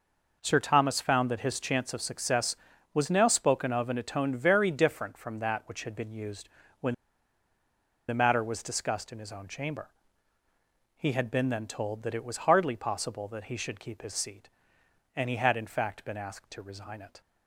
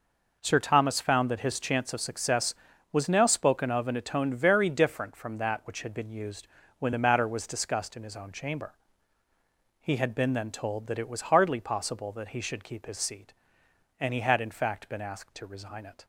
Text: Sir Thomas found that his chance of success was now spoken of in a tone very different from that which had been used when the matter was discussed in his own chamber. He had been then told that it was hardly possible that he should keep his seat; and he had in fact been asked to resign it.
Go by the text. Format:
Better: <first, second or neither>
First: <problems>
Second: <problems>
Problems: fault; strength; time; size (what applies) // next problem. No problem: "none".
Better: second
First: pauses between "used" and "when"; slight; at 6.4 s; 0.32 s long // pauses between "when" and "the"; at 6.9 s; 1.1 s long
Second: pauses between "used" and "when"; slight; at 6.4 s; 0.32 s long